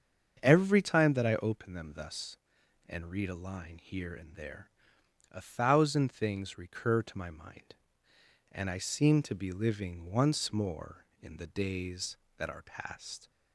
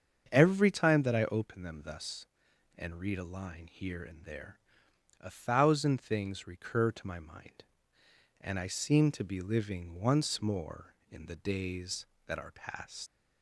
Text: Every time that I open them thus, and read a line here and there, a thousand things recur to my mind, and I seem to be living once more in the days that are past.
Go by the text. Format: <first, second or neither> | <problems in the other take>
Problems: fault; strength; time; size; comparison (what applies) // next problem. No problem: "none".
first | starts louder than the rest; until 1.3 s; 7 dB; also in the first // leaves "past" unfinished; at 13.0 s; 125 ms